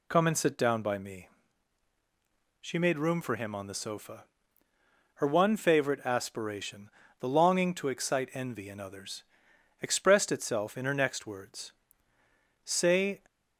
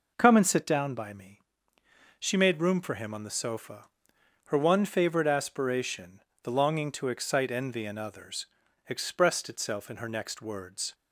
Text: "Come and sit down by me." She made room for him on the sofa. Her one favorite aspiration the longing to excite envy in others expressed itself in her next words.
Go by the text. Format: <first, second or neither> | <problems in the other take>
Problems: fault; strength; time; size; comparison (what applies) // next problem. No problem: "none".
second | pauses between "aspiration" and "the"; slight; at 6.8 s; 0.30 s long; slight in the second // pauses between "others" and "expressed"; noticeable; at 9.2 s; 0.58 s long; also in the second // goes on to say "Say"; from 12.6 s on; 0.58 s long